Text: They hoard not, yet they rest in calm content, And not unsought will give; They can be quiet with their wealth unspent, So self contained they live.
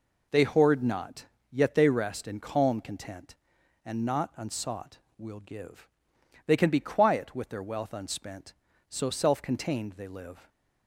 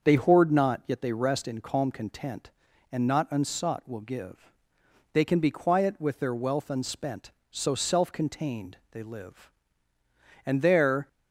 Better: first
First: none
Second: starts louder than the rest; until 1.0 s; 6.5 dB // goes on to say "And there"; noticeable; from 10.4 s on; 0.64 s long

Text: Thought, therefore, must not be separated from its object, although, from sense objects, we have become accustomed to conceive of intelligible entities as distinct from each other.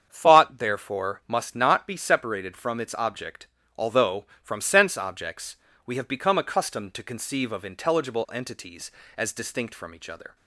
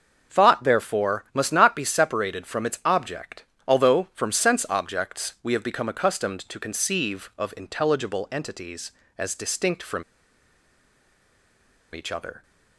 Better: first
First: starts louder than the rest; strong; until 1.1 s; 7.5 dB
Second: starts louder than the rest; until 1.3 s; 6.5 dB // pauses between "from" and "each"; strong; at 10.0 s; 1.9 s long

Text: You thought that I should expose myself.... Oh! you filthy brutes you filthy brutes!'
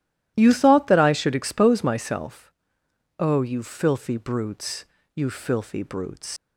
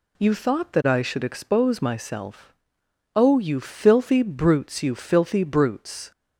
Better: second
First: pauses between "brutes" and "you"; slight; at 4.8 s; 0.30 s long // leaves "brutes" unfinished; at 6.3 s; 125 ms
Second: none

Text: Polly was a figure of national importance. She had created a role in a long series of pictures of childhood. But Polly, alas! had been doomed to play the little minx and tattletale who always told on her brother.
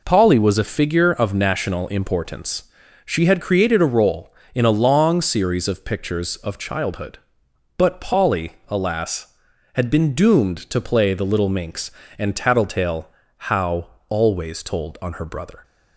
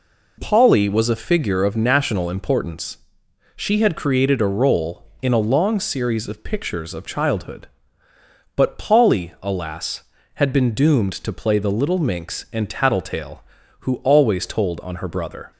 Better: second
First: says "how" for "who"; at 13.4 s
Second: none

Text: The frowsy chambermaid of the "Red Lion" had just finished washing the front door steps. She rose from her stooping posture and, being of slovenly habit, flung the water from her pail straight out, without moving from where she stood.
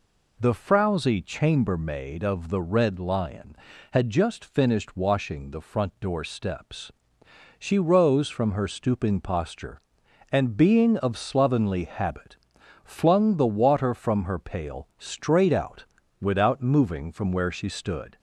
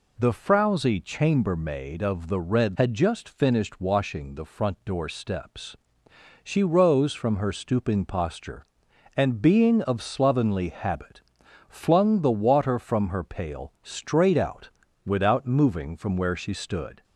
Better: first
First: none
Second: skips "Lion"; at 2.7 s

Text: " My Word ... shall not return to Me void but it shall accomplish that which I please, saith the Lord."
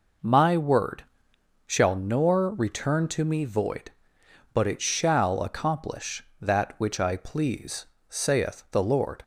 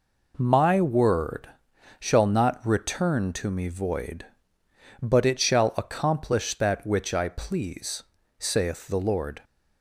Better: second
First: says "nor" for "not"; at 1.9 s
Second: none

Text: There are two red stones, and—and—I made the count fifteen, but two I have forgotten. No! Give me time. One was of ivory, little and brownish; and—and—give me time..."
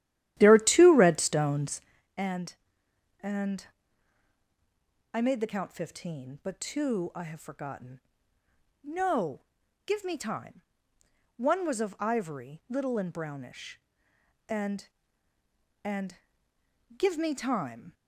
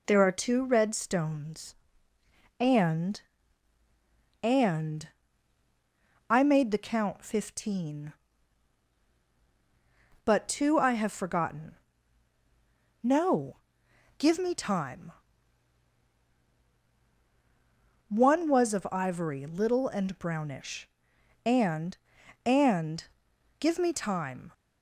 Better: second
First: starts louder than the rest; strong; until 1.9 s; 12.5 dB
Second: none

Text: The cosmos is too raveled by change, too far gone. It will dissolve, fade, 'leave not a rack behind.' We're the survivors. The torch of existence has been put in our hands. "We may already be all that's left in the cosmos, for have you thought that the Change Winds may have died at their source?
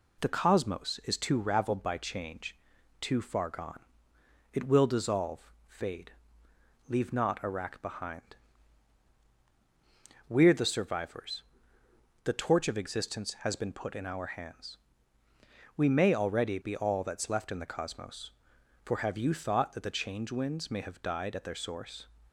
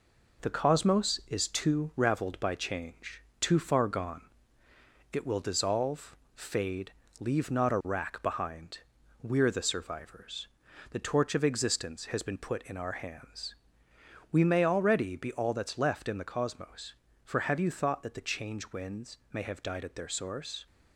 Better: first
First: none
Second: gets quieter; noticeable; throughout; 5 dB // pauses between "Winds" and "may"; slight; at 19.1 s; 0.16 s long

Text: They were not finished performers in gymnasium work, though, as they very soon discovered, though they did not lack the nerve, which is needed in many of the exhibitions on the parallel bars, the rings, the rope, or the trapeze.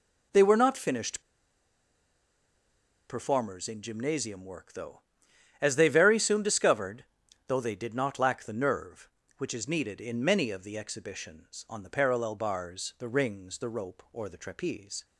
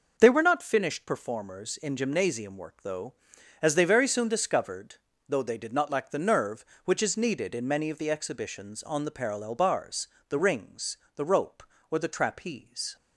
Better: second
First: pauses between "finished" and "performers"; strong; at 1.2 s; 1.8 s long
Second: none

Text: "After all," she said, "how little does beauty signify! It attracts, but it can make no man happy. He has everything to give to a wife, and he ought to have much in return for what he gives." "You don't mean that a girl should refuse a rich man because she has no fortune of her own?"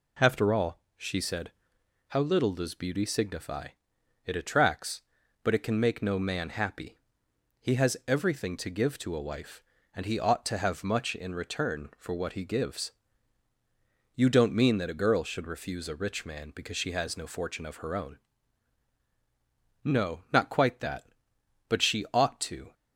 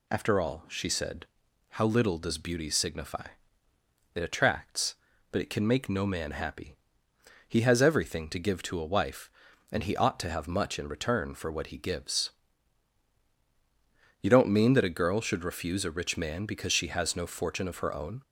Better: second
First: goes on to say "No not quite that But she ought to"; strong; from 19.8 s on; 2.9 s long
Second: none

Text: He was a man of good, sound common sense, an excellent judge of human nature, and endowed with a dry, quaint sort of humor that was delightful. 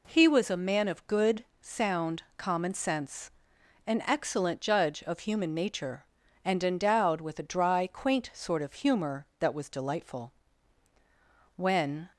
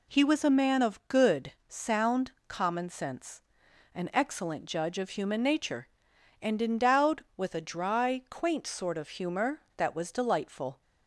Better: second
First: pauses between "sound" and "common"; slight; at 2.2 s; 0.16 s long // goes on to say "When"; from 11.5 s on; 0.56 s long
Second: pauses between "sound" and "common"; slight; at 2.3 s; 0.16 s long

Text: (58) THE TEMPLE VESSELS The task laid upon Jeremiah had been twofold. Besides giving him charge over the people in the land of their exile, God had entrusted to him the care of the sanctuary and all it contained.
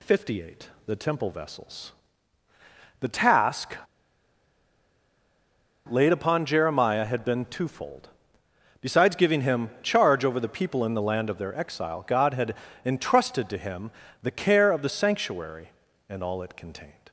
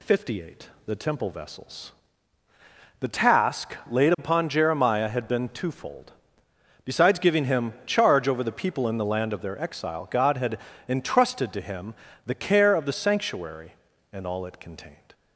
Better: second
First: pauses between "VESSELS" and "The"; at 1.9 s; 1.0 s long // pauses between "task" and "laid"; strong; at 3.7 s; 2.1 s long // pauses between "had" and "entrusted"; slight; at 12.5 s; 0.28 s long // pauses between "him" and "the"; slight; at 13.9 s; 0.32 s long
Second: pauses between "VESSELS" and "The"; at 1.9 s; 1.0 s long // pauses between "had" and "entrusted"; slight; at 10.5 s; 0.28 s long // pauses between "him" and "the"; slight; at 11.9 s; 0.32 s long

